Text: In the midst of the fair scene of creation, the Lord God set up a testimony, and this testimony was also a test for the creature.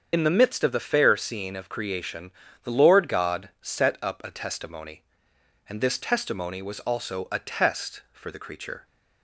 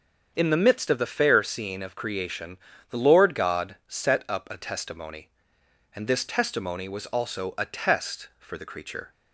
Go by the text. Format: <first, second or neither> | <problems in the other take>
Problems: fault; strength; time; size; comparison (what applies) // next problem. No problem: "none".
second | loses the start of "In"; at 0.1 s; 50 ms // starts louder than the rest; strong; until 1.1 s; 7 dB; also in the second